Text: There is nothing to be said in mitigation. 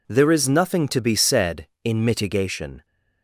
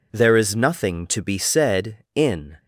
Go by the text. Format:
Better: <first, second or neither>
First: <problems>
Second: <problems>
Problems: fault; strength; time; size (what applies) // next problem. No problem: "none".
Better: first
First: none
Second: stops before "mitigation"; at 2.5 s